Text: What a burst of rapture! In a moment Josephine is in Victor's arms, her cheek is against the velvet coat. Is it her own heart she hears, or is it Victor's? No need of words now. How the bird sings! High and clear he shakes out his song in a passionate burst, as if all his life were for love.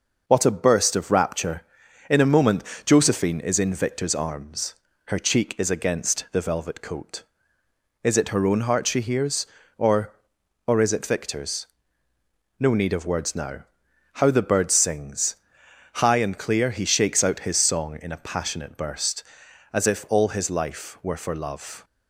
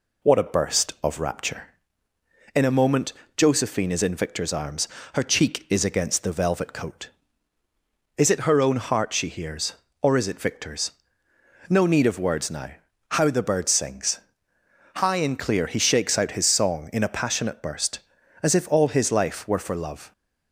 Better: second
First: pauses between "moment" and "Josephine"; slight; at 2.6 s; 0.22 s long // says "or" twice; at 10.6 s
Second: pauses between "moment" and "Josephine"; slight; at 3.1 s; 0.24 s long

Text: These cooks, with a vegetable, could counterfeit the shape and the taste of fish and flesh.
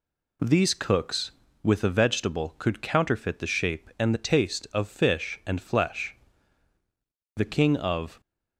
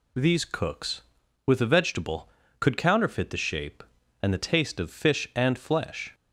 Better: second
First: goes on to say "The king of"; noticeable; from 7.3 s on; 0.84 s long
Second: none

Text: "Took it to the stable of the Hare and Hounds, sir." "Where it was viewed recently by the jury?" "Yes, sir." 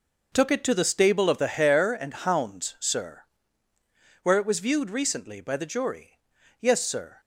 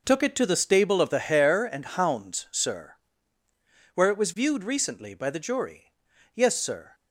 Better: neither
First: none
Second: none

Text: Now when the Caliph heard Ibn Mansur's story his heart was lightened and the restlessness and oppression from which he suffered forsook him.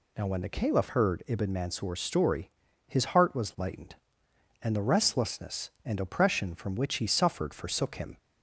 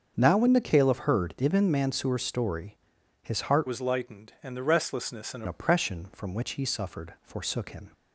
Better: first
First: pauses between "story" and "his"; at 2.4 s; 0.38 s long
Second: starts louder than the rest; until 1.1 s; 7 dB // pauses between "story" and "his"; noticeable; at 2.7 s; 0.48 s long // changes voice from "was" to "and"; from 3.6 to 5.4 s; 1.8 s long

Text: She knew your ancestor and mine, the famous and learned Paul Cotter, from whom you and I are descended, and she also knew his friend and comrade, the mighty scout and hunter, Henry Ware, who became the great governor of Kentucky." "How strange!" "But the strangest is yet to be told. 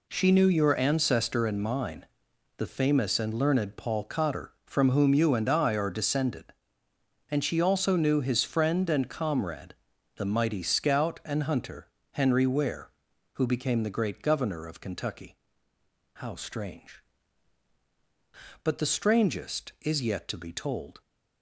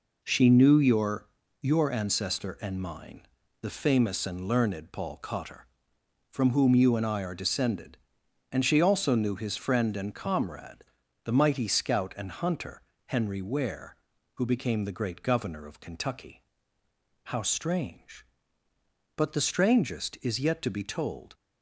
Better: first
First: none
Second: says "your" twice; at 1.6 s

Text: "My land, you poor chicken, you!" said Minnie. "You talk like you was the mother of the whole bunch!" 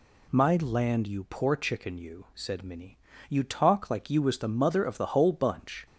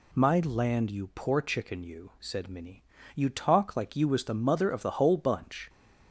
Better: neither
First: none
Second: none

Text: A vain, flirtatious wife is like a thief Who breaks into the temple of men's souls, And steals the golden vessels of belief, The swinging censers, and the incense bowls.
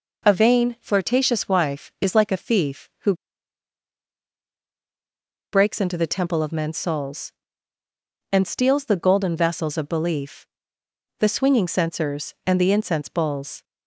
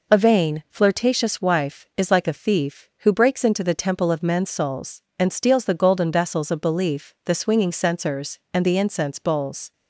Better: second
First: pauses between "Who" and "breaks"; strong; at 3.1 s; 2.3 s long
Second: none

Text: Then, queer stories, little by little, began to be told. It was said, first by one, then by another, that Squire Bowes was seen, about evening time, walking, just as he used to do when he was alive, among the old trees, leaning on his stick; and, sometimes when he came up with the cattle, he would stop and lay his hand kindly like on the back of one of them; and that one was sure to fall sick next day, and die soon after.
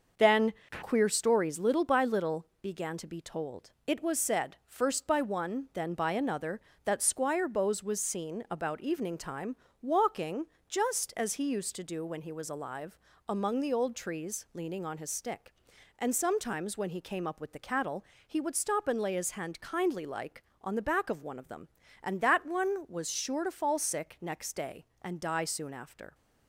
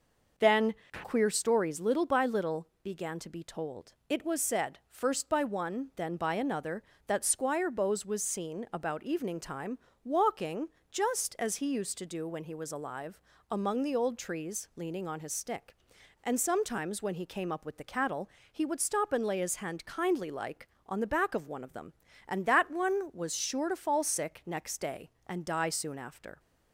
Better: second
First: gets quieter; noticeable; throughout; 5.5 dB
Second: none

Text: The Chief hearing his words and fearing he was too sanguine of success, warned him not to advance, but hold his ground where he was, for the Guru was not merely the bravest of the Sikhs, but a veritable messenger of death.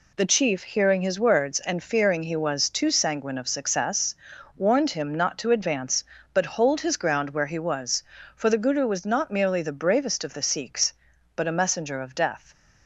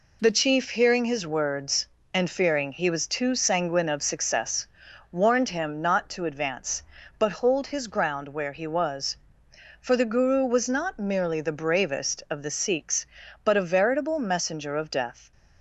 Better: second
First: skips "veritable"; at 11.5 s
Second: none

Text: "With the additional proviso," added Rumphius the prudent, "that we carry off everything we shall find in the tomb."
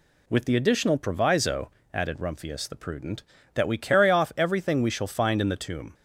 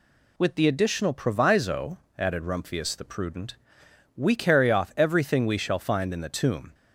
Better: first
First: none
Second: skips "that"; at 3.8 s

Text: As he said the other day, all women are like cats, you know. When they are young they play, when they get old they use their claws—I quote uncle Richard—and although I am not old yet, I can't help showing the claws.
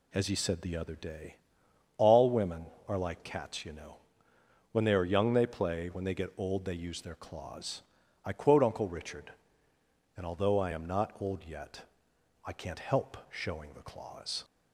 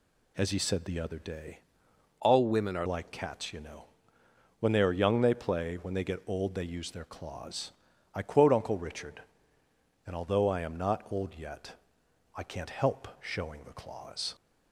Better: first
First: none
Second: changes voice from "all" to "are"; from 2.1 to 2.8 s; 0.7 s long

